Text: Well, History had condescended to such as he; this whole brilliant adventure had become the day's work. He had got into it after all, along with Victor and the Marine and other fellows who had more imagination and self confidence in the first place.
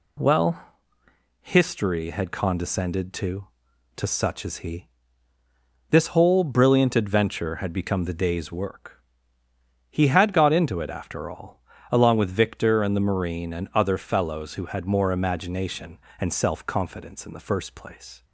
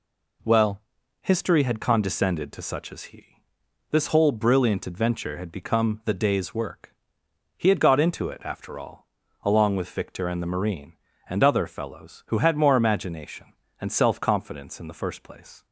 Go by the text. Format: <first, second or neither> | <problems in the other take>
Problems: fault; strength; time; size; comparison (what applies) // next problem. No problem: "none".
second | says "to" twice; at 3.9 s